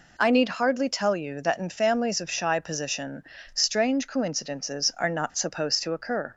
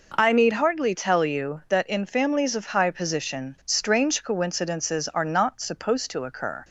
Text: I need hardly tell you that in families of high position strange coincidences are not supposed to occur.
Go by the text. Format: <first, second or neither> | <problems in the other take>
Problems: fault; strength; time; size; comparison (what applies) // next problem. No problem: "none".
second | says "shy" for "high"; at 2.2 s // pauses between "position" and "strange"; slight; at 3.2 s; 0.28 s long